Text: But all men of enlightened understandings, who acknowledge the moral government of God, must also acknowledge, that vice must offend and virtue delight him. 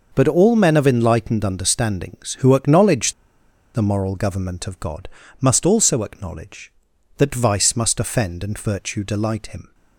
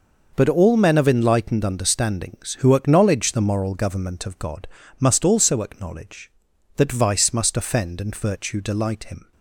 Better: second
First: pauses between "acknowledge" and "the"; noticeable; at 3.1 s; 0.61 s long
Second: none

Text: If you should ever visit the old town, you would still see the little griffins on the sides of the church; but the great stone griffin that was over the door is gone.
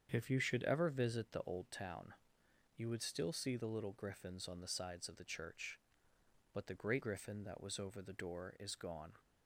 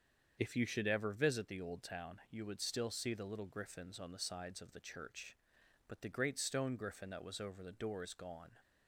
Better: second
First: starts louder than the rest; strong; until 1.1 s; 7.5 dB // skips "stone"; at 7.0 s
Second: starts louder than the rest; strong; until 1.4 s; 7 dB

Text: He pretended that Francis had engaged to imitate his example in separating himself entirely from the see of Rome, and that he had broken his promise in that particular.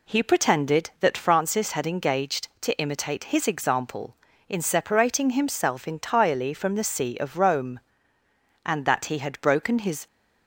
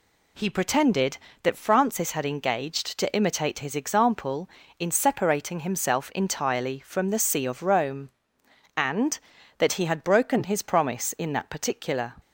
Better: second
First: stops before "promise in that particular"; at 10.0 s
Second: none

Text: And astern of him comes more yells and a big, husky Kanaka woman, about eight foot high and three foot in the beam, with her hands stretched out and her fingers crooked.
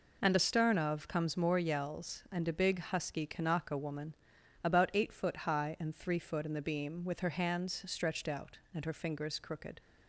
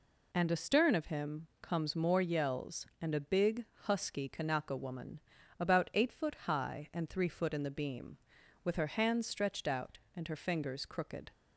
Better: second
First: skips "him"; at 1.0 s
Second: none

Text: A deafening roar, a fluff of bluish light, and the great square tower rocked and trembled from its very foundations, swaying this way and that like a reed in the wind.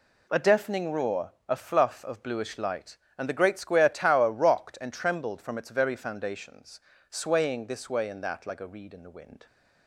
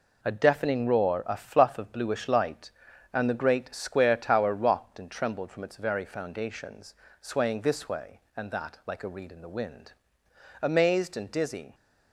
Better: first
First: none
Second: goes on to say "Amazed and dizzy"; noticeable; from 10.6 s on; 1.1 s long

